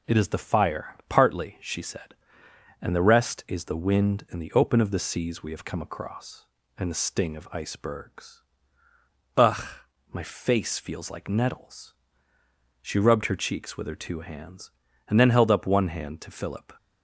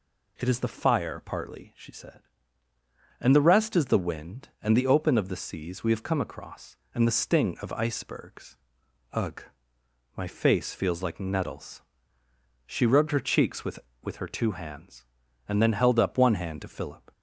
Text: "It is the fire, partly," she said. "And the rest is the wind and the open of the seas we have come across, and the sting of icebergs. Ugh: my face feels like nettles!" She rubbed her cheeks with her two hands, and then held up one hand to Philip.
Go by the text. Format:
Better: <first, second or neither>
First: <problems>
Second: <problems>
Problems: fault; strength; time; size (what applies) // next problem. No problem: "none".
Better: first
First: none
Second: says "with" twice; at 14.0 s